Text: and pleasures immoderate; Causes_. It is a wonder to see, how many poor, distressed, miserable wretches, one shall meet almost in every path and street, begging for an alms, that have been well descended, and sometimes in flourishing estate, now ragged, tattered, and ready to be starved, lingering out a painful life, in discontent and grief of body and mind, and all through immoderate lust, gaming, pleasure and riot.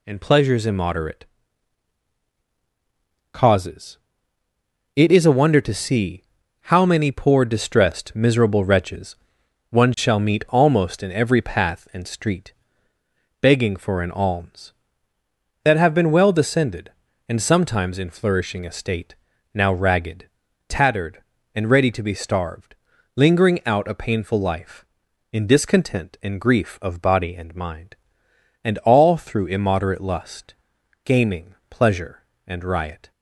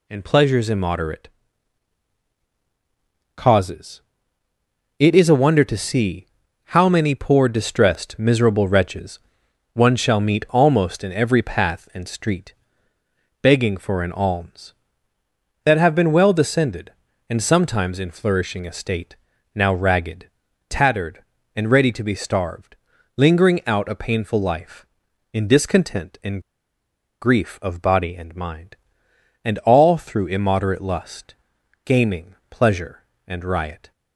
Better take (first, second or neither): first